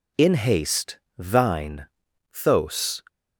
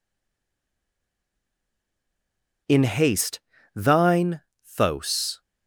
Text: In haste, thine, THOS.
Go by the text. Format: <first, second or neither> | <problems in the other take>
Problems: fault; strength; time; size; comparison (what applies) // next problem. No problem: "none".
first | stays silent before the first word; strong; until 2.6 s; 2.6 s long